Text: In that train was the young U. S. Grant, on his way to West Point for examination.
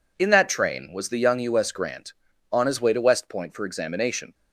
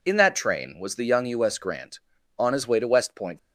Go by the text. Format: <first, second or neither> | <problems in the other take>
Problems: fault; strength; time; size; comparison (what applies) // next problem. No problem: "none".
first | stops before "for examination"; at 3.3 s